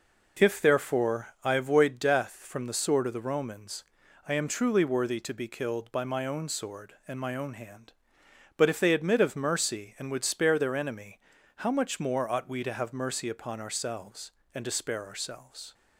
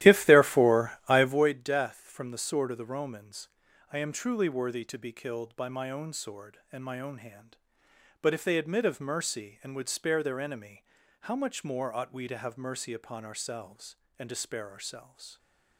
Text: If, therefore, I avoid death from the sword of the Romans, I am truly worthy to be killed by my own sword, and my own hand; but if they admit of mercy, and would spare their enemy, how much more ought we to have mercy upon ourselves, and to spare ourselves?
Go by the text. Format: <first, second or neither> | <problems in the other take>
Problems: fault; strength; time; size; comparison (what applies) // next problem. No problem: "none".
first | starts louder than the rest; strong; until 1.4 s; 13.5 dB